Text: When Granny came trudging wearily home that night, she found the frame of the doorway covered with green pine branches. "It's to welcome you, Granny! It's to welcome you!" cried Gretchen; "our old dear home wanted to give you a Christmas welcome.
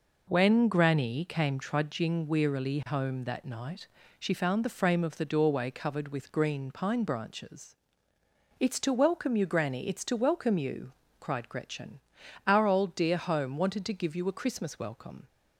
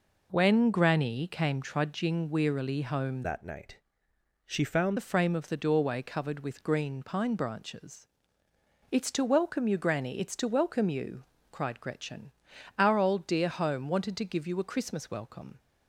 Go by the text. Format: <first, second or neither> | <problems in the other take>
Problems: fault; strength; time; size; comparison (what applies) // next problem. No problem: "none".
first | changes voice from "that" to "found"; from 3.2 to 4.9 s; 1.7 s long